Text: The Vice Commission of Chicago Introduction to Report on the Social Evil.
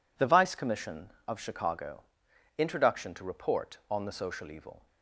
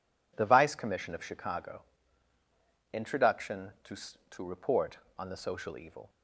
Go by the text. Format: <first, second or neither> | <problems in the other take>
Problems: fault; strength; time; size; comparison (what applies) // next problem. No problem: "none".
first | pauses between "Chicago" and "Introduction"; at 1.8 s; 1.1 s long; noticeable in the first // says "to" twice; at 4.3 s